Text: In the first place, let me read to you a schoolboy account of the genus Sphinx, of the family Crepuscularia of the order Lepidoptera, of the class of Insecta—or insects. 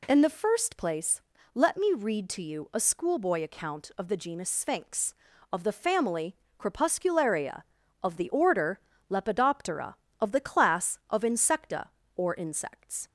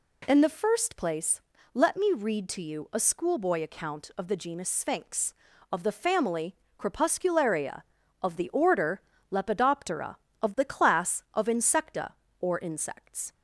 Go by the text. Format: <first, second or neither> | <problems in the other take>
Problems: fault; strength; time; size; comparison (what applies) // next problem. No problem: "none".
neither | pauses between "family" and "Crepuscularia"; slight; the same in both // pauses between "order" and "Lepidoptera"; slight; the same in both